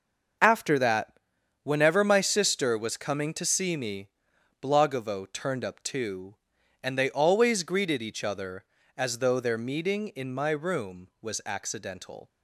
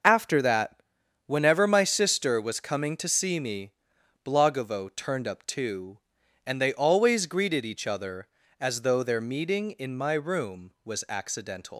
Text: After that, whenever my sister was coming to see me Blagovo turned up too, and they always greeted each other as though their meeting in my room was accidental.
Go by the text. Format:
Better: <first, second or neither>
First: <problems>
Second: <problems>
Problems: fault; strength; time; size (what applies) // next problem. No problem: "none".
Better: first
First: starts louder than the rest; noticeable; until 1.8 s; 6 dB // pauses between "me" and "Blagovo"; noticeable; at 4.0 s; 0.54 s long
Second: starts louder than the rest; noticeable; until 1.5 s; 6 dB // pauses between "me" and "Blagovo"; noticeable; at 3.7 s; 0.54 s long // leaves "accidental" unfinished; at 11.7 s; 120 ms